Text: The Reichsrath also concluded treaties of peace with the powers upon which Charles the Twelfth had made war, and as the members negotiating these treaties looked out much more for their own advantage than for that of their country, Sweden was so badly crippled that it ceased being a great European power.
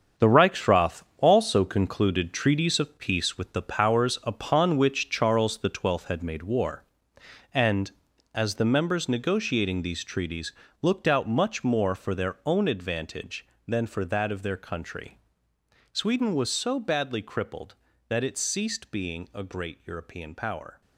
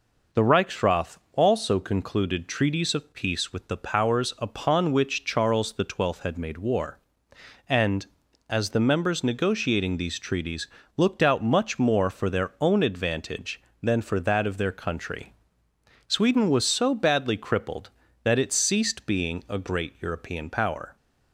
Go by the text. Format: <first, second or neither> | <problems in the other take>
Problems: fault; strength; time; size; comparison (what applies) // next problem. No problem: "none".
second | gets quieter; strong; throughout; 9.5 dB // pauses between "Reichsrath" and "also"; slight; at 1.0 s; 0.16 s long; slight in the second // pauses between "treaties" and "looked"; slight; at 10.5 s; 0.28 s long; slight in the second